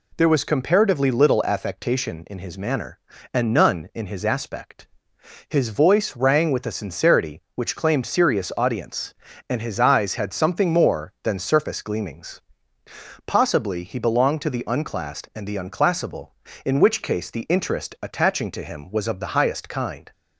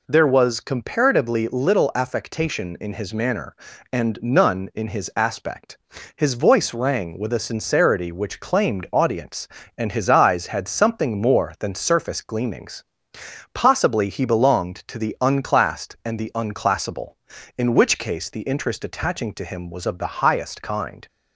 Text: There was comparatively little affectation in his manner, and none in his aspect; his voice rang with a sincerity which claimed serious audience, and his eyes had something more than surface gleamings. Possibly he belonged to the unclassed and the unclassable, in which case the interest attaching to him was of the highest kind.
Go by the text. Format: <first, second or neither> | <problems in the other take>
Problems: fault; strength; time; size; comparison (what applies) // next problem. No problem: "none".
first | skips "serious"; at 8.8 s